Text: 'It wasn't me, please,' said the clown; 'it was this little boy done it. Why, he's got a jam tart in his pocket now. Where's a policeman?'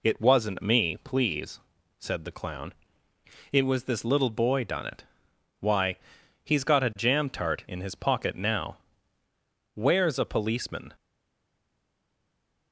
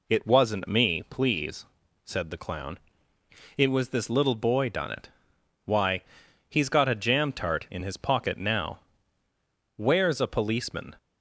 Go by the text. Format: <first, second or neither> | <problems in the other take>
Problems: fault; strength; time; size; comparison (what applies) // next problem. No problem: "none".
second | stays silent after the last word; noticeable; from 10.9 s on; 1.8 s long